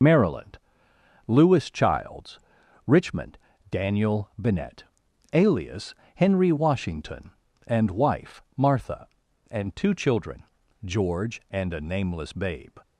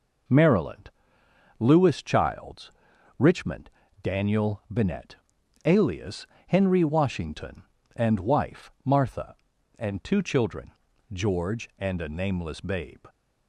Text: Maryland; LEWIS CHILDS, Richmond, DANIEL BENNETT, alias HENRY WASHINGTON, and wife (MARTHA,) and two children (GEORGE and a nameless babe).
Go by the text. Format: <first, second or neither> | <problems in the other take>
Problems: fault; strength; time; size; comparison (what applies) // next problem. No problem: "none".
second | loses the start of "Maryland"; at 0.0 s; 50 ms // pauses between "alias" and "HENRY"; slight; at 5.9 s; 0.22 s long; slight in the second